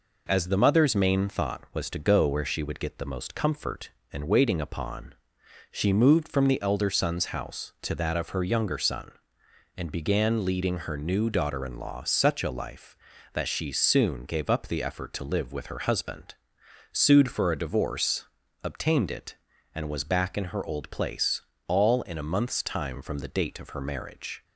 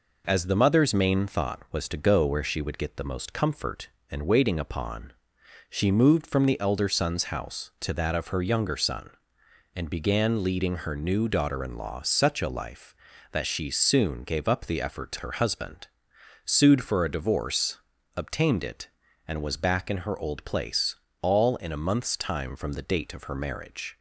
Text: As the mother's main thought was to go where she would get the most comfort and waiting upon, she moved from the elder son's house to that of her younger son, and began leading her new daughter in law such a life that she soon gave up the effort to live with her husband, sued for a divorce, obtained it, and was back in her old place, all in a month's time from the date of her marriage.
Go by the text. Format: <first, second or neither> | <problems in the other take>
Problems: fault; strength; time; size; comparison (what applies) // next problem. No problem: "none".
first | skips "live with"; at 15.1 s